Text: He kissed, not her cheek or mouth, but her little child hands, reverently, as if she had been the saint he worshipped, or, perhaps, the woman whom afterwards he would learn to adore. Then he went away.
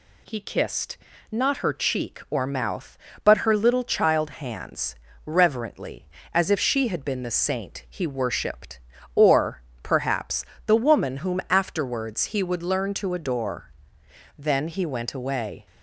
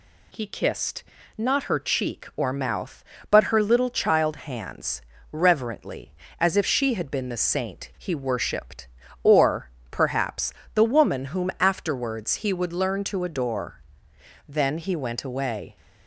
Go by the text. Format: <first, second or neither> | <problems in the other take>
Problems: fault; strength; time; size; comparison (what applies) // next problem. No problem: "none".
neither | none